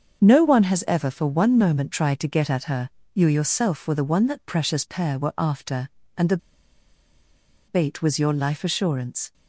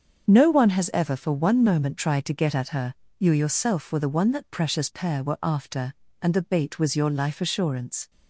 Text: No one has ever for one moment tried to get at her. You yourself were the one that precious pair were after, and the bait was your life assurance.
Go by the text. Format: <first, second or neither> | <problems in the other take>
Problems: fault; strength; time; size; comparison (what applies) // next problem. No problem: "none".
second | starts louder than the rest; until 1.2 s; 7 dB; also in the second // pauses between "the" and "bait"; strong; at 6.3 s; 1.3 s long